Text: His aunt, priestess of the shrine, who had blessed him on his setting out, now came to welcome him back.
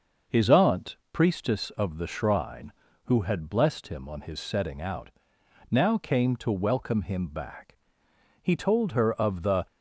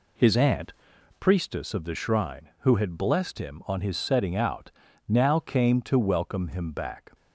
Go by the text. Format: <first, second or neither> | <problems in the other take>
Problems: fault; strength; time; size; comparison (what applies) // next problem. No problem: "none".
second | starts louder than the rest; noticeable; until 1.4 s; 6 dB // goes on to say "He told her of the"; noticeable; from 8.4 s on; 1.2 s long